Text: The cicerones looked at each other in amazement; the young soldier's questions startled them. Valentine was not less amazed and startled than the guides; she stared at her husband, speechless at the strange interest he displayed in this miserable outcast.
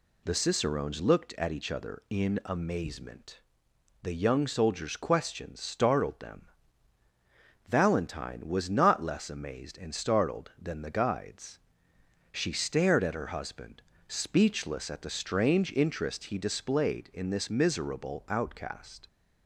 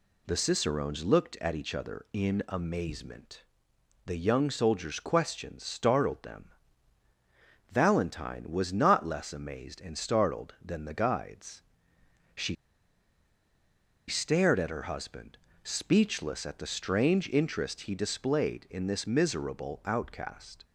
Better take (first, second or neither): first